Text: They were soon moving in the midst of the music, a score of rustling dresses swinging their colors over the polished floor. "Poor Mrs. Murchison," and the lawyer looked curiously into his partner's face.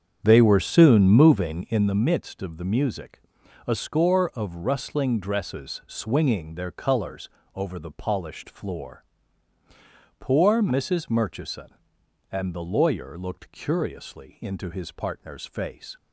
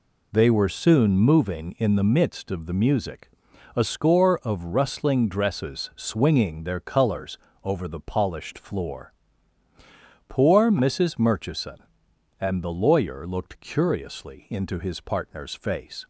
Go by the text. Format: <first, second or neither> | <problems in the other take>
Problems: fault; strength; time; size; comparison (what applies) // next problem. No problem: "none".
second | starts louder than the rest; strong; until 1.9 s; 8 dB // pauses between "colors" and "over"; slight; at 7.2 s; 0.28 s long; slight in the second